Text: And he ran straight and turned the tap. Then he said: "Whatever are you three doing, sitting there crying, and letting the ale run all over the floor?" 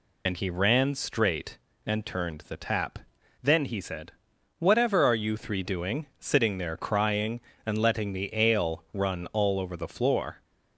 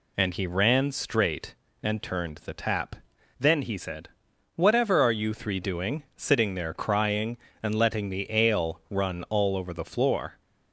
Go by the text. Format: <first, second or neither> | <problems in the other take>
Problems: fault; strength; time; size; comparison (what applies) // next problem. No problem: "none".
second | loses the start of "And"; at 0.2 s; 55 ms